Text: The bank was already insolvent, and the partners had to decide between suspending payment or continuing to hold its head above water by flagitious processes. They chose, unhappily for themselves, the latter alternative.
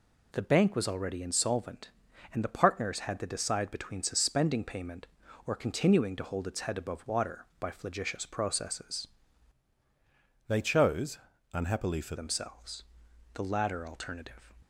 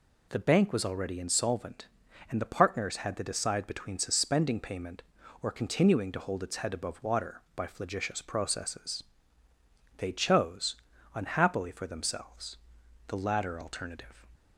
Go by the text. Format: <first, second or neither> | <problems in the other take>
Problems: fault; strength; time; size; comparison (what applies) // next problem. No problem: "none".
second | changes voice from "They" to "for"; from 10.4 to 12.1 s; 1.7 s long